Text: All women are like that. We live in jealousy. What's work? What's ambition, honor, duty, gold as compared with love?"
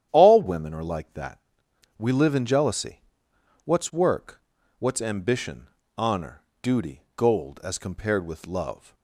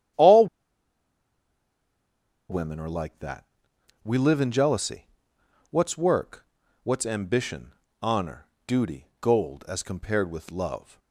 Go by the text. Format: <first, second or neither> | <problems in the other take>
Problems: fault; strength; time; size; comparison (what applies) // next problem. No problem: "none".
first | starts louder than the rest; strong; until 3.2 s; 10 dB; strong in the first // pauses between "All" and "women"; strong; at 0.4 s; 2.0 s long